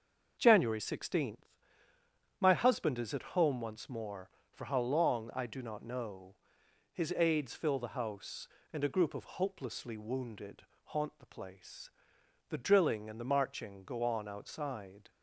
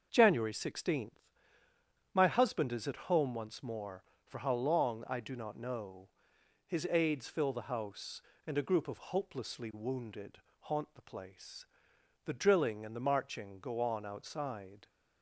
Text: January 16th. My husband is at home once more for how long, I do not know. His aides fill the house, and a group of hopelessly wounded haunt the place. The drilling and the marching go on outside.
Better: neither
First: starts louder than the rest; until 1.3 s; 6.5 dB // pauses between "wounded" and "haunt"; slight; at 10.6 s; 0.22 s long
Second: starts louder than the rest; until 1.1 s; 6.5 dB // pauses between "wounded" and "haunt"; slight; at 10.3 s; 0.22 s long

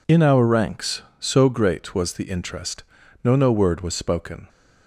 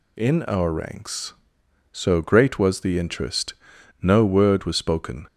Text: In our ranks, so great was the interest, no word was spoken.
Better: second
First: says "no" twice; at 3.3 s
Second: none

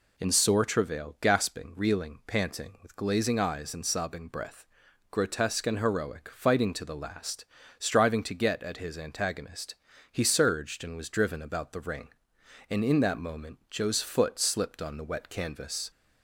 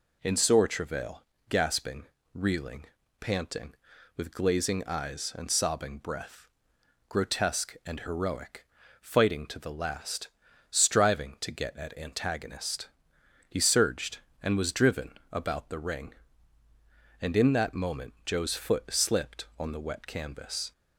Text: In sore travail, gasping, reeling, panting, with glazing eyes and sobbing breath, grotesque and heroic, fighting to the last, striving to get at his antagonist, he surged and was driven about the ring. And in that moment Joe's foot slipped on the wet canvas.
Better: first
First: none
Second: skips "his"; at 11.9 s // pauses between "driven" and "about"; slight; at 15.1 s; 0.20 s long

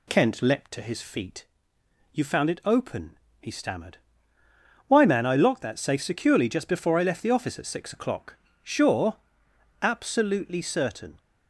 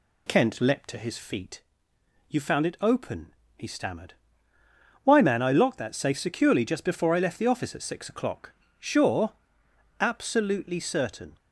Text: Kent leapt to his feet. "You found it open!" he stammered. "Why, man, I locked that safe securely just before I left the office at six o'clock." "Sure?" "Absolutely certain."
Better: neither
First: none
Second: none

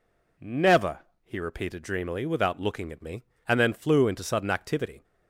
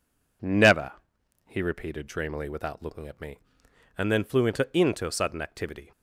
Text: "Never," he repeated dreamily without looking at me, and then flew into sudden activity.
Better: first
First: none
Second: says "into" twice; at 4.7 s

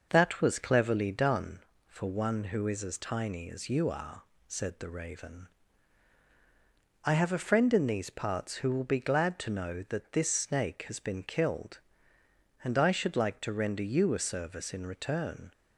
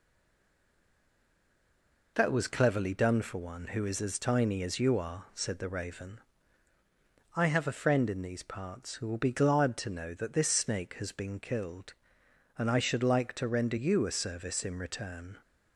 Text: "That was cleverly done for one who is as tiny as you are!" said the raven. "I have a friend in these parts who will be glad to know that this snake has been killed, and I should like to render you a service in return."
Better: first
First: none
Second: stays silent before the first word; until 2.1 s; 2.1 s long

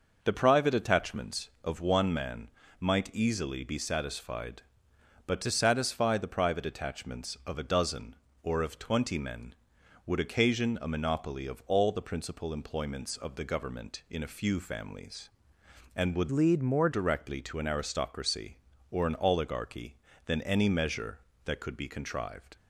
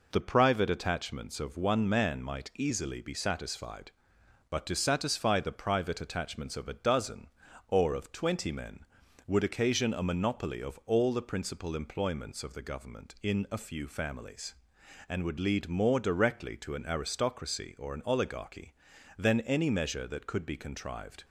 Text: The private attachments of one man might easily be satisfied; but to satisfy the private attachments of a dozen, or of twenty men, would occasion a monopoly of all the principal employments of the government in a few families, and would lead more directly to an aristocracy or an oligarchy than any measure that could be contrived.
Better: second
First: pauses between "man" and "might"; slight; at 2.4 s; 0.30 s long // changes voice from "lead" to "more"; from 16.3 to 16.8 s; 0.5 s long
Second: none

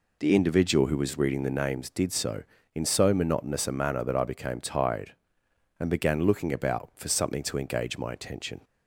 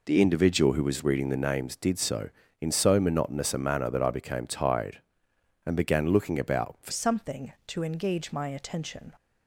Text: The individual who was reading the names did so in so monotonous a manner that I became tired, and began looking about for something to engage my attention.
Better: first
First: none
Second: changes voice at "something"; from 6.9 s on; 2.2 s long

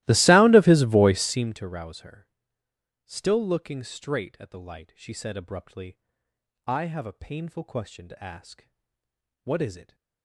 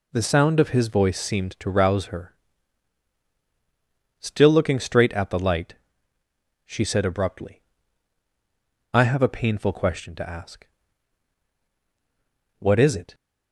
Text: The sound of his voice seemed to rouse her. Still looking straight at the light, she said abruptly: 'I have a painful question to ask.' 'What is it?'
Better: second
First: starts louder than the rest; strong; until 1.6 s; 17.5 dB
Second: none

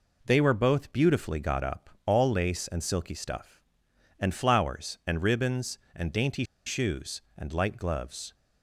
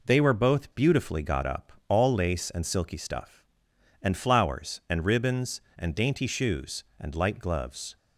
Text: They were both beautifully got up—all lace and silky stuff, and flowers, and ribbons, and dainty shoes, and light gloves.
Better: second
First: pauses between "dainty" and "shoes"; slight; at 6.4 s; 0.22 s long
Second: none

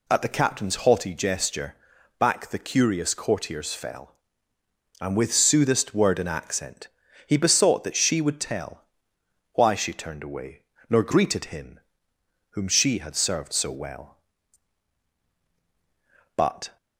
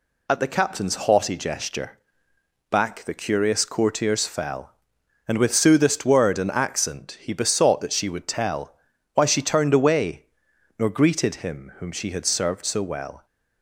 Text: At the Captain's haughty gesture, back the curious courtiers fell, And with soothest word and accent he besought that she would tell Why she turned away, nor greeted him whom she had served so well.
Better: second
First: pauses between "accent" and "he"; at 6.8 s; 0.40 s long // pauses between "tell" and "Why"; noticeable; at 8.8 s; 0.68 s long // pauses between "him" and "whom"; noticeable; at 11.8 s; 0.70 s long // goes on to say "But"; slight; from 16.3 s on; 0.40 s long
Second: pauses between "tell" and "Why"; at 8.7 s; 0.42 s long

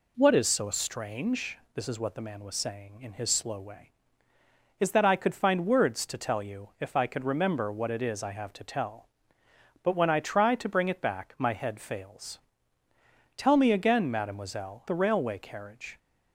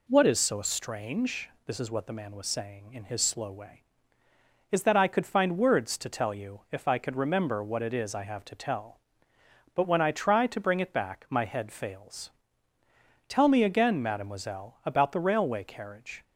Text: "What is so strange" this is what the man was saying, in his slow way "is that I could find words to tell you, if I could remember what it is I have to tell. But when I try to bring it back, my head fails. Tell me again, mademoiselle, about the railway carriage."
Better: second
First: pauses between "strange" and "this"; slight; at 1.5 s; 0.16 s long // skips "about"; at 14.8 s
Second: pauses between "strange" and "this"; slight; at 1.4 s; 0.16 s long

